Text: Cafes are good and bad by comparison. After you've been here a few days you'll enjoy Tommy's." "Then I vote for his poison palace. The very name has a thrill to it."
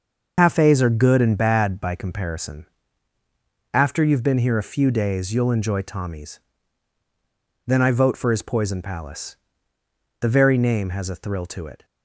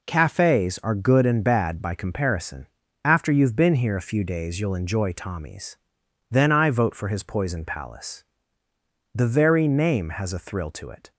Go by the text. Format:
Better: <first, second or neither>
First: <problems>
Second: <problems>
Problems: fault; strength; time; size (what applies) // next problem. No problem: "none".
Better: second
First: loses the start of "Cafes"; at 0.3 s; 100 ms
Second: none